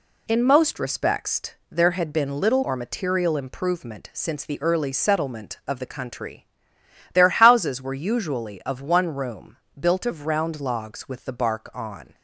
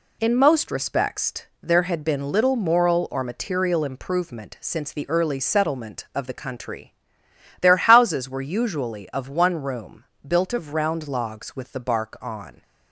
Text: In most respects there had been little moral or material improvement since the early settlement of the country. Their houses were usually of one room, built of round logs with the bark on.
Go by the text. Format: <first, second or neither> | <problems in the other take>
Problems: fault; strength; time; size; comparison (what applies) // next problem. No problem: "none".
second | pauses between "respects" and "there"; slight; at 1.5 s; 0.18 s long; slight in the second // skips "moral"; at 2.6 s